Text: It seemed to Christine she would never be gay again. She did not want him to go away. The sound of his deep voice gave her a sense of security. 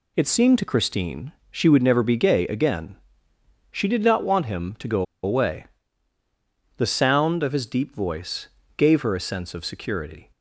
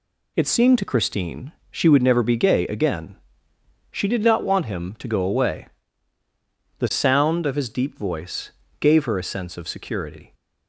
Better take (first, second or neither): second